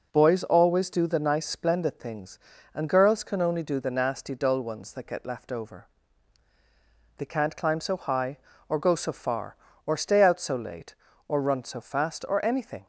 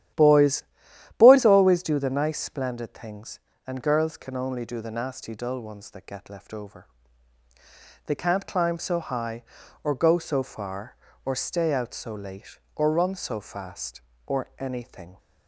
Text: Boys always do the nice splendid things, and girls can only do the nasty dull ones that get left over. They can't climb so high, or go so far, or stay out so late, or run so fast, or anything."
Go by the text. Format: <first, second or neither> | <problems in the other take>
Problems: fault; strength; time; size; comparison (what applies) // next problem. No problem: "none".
first | starts louder than the rest; strong; until 1.7 s; 11.5 dB // says "Boys" twice; at 1.1 s